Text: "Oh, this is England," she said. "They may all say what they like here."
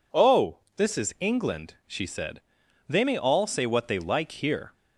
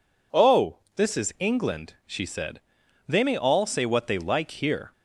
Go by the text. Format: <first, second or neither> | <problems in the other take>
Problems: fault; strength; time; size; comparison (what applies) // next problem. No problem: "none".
neither | none